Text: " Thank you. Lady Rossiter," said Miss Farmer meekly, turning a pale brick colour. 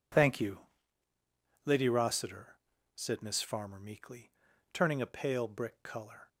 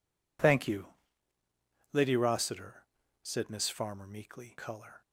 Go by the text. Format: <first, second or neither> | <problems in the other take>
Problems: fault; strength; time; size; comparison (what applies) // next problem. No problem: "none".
first | skips "turning a pale brick"; at 4.5 s